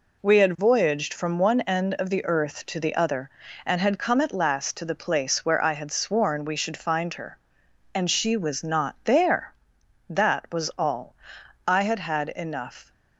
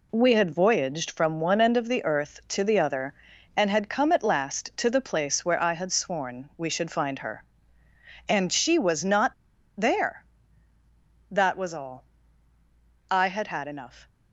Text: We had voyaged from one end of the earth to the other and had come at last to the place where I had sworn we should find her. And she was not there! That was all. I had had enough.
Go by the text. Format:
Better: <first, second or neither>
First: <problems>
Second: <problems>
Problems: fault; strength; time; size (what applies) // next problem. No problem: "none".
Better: first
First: none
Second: pauses between "not" and "there"; noticeable; at 9.3 s; 0.46 s long